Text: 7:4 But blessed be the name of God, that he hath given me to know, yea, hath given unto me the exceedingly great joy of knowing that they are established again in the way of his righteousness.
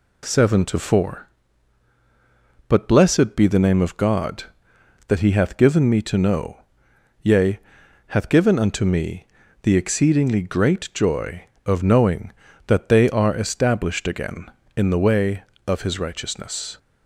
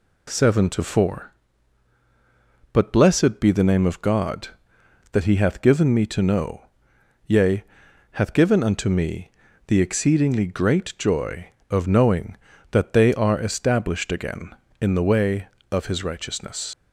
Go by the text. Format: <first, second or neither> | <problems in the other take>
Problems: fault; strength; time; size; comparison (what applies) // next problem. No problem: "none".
first | pauses between "me" and "the"; at 9.3 s; 0.38 s long; also in the first // leaves "righteousness" unfinished; at 16.7 s; 90 ms